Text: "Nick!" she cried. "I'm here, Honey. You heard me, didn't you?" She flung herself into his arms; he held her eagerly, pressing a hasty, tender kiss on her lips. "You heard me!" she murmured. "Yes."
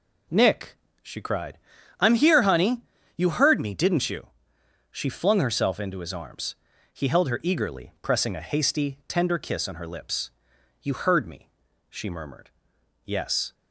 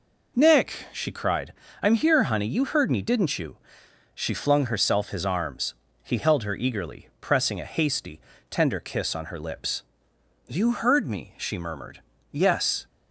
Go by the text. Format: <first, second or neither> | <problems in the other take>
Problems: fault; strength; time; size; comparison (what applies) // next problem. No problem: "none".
first | skips "into"; at 5.0 s